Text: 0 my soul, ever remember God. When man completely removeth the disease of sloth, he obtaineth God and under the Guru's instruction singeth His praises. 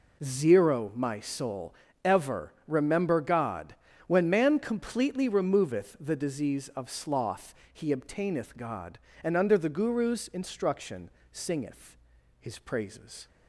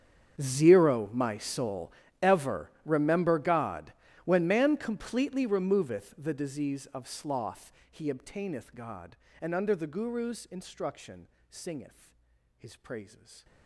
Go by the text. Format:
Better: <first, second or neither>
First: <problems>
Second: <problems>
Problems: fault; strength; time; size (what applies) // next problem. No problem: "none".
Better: first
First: pauses between "instruction" and "singeth"; slight; at 11.1 s; 0.22 s long // pauses between "singeth" and "His"; at 11.9 s; 0.42 s long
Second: gets quieter; strong; throughout; 23 dB // pauses between "instruction" and "singeth"; slight; at 11.2 s; 0.22 s long // pauses between "singeth" and "His"; at 12.1 s; 0.42 s long